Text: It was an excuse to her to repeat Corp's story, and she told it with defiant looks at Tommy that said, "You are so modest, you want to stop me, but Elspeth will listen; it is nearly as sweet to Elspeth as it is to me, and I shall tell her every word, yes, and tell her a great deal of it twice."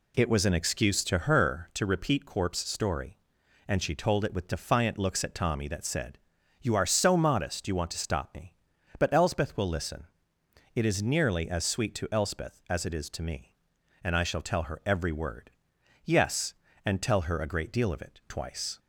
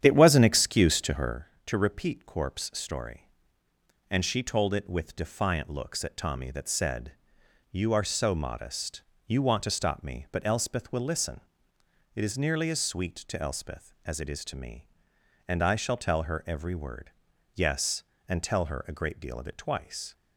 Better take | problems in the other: first | starts louder than the rest; strong; until 1.4 s; 9.5 dB

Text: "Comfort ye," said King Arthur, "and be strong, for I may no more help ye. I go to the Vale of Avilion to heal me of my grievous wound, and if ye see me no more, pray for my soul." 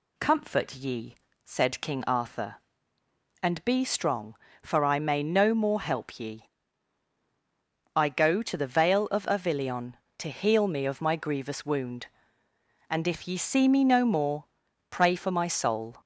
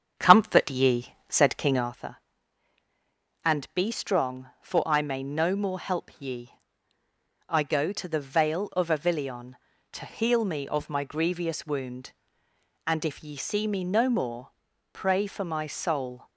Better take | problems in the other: first | starts louder than the rest; strong; until 1.9 s; 7.5 dB

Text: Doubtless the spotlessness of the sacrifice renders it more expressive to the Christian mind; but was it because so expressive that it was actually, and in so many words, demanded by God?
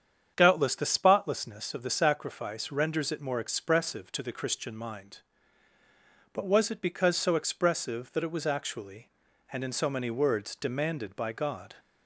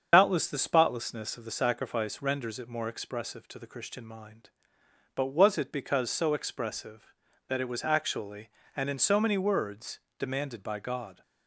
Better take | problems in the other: first | loses the start of "Doubtless"; at 0.1 s; 75 ms // starts louder than the rest; strong; until 1.1 s; 7.5 dB; strong in the first

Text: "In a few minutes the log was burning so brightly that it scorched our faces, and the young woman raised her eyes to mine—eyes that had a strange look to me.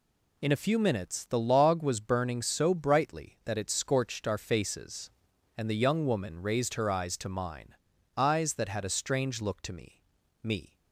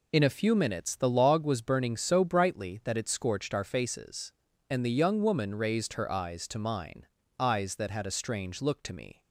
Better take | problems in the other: second | says "me" twice; at 10.4 s

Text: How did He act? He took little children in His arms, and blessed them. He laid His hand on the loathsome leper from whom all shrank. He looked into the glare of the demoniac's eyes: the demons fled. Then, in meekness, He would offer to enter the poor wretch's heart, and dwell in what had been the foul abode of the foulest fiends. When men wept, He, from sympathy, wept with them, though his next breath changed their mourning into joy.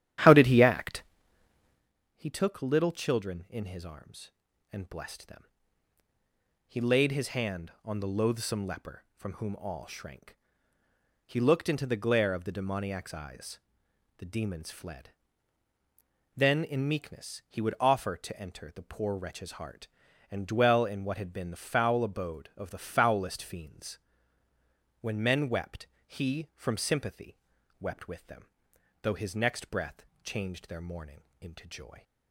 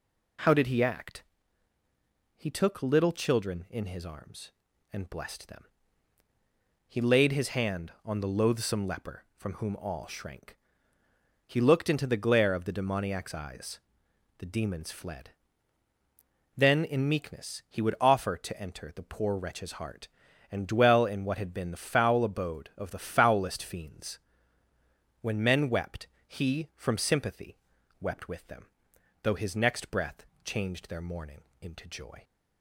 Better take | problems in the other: second | starts louder than the rest; strong; until 1.9 s; 11 dB // pauses between "breath" and "changed"; slight; at 30.0 s; 0.18 s long; slight in the second // pauses between "mourning" and "into"; slight; at 31.2 s; 0.20 s long; slight in the second

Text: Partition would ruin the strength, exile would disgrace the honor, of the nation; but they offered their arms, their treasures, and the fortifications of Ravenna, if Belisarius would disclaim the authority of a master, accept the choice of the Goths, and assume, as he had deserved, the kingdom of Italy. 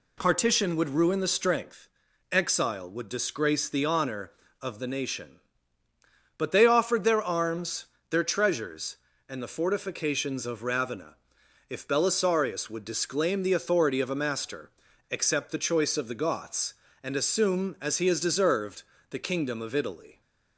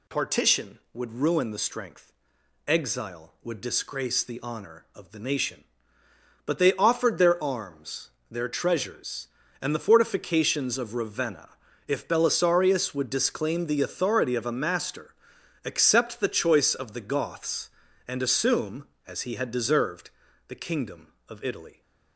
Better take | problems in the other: second | says "has" for "had"; at 18.0 s

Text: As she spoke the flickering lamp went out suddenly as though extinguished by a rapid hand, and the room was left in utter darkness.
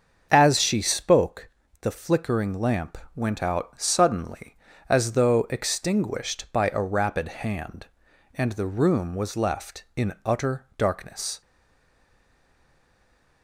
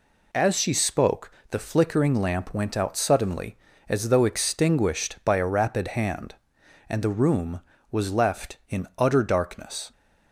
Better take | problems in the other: second | starts louder than the rest; until 1.3 s; 7 dB // pauses between "spoke" and "the"; slight; at 1.4 s; 0.32 s long; slight in the second // pauses between "lamp" and "went"; slight; at 2.9 s; 0.16 s long // stays silent after the last word; noticeable; from 11.4 s on; 2.0 s long

